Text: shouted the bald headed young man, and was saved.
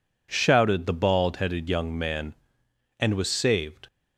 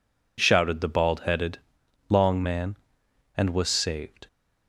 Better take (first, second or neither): first